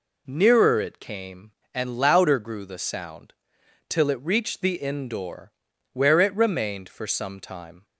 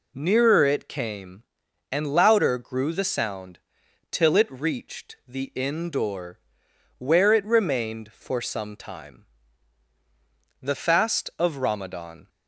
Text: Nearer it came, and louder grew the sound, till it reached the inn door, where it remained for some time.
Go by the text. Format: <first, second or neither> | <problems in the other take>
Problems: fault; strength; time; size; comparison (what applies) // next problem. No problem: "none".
first | goes on to say "The fast of Ramadan"; from 10.6 s on; 1.6 s long